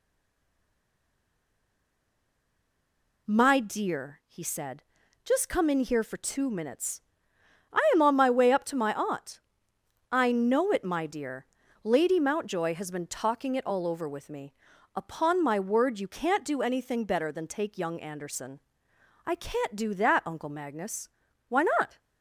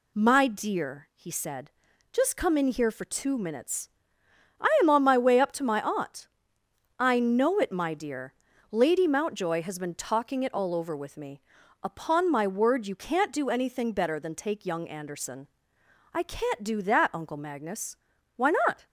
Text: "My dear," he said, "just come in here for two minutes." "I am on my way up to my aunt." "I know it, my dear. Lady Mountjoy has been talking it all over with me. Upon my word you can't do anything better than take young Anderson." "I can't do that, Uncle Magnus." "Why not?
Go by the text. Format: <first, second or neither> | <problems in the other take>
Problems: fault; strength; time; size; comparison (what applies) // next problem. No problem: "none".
second | stays silent before the first word; strong; until 3.2 s; 3.2 s long